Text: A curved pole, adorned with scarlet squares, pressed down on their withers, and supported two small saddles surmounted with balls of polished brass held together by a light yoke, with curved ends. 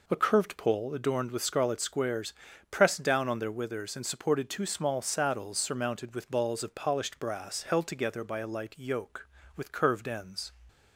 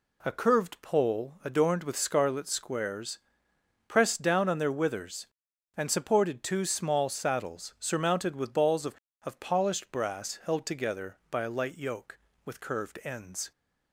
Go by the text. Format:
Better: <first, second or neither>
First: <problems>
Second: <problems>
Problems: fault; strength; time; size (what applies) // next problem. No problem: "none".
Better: first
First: none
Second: says "of" twice; at 9.2 s